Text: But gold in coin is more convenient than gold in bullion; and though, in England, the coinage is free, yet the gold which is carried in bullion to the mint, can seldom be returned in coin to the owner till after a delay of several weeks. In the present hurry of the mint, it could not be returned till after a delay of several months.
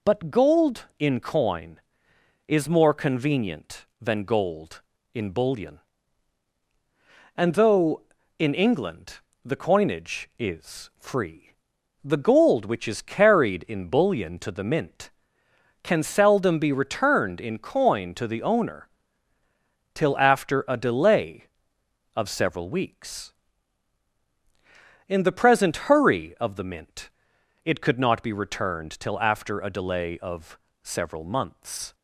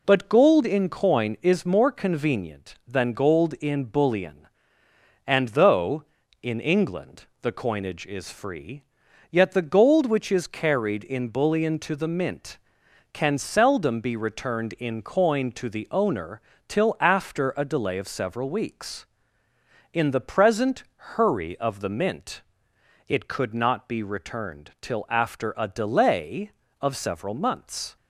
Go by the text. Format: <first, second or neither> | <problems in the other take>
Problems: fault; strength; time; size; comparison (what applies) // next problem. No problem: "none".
second | skips "yet"; at 11.7 s // pauses between "owner" and "till"; at 18.8 s; 1.0 s long; slight in the second // pauses between "of" and "several"; slight; at 30.5 s; 0.24 s long